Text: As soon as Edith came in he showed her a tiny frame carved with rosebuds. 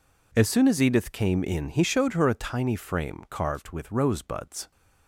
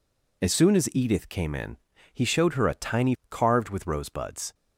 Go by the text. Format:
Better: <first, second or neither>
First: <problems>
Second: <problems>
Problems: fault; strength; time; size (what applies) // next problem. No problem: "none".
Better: first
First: none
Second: pauses between "in" and "he"; slight; at 1.7 s; 0.36 s long // skips "frame"; at 3.2 s